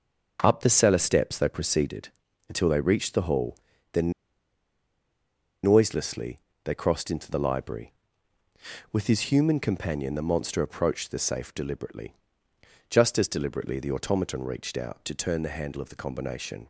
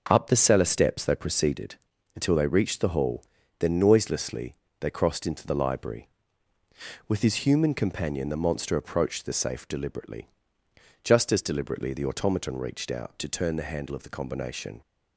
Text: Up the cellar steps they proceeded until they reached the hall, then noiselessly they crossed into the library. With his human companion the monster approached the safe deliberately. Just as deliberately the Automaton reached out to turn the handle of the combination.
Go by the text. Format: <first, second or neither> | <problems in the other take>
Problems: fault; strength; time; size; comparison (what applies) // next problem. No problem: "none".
second | starts louder than the rest; noticeable; until 1.4 s; 6 dB // pauses between "proceeded" and "until"; at 2.0 s; 0.40 s long; also in the second // pauses between "then" and "noiselessly"; strong; at 4.1 s; 1.5 s long // pauses between "noiselessly" and "they"; slight; at 6.3 s; 0.26 s long; slight in the second